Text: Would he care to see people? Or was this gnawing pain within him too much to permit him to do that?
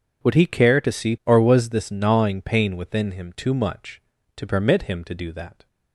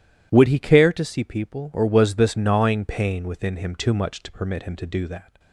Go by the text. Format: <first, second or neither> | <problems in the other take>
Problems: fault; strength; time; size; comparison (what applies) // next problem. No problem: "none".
second | skips "people"; at 1.2 s